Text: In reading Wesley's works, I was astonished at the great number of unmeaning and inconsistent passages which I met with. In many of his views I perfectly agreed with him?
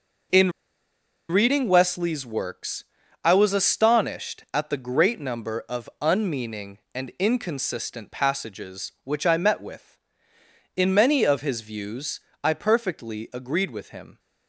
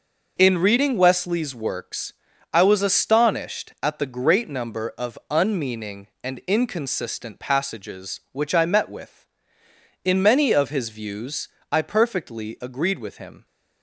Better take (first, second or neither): second